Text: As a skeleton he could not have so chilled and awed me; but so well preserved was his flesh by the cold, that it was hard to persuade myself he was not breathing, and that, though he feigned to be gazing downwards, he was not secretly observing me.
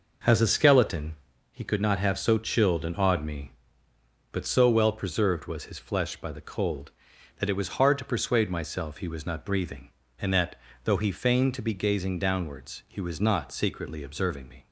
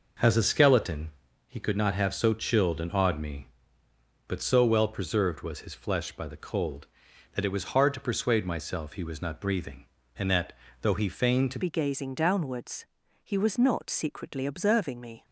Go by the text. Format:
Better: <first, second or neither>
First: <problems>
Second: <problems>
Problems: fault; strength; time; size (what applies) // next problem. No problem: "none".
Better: first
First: pauses between "skeleton" and "he"; slight; at 1.1 s; 0.34 s long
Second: pauses between "skeleton" and "he"; slight; at 1.1 s; 0.34 s long // changes voice at "be"; from 11.6 s on; 3.6 s long